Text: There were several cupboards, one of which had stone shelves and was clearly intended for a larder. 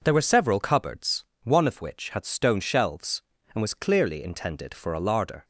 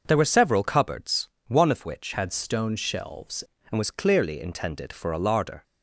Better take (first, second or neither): first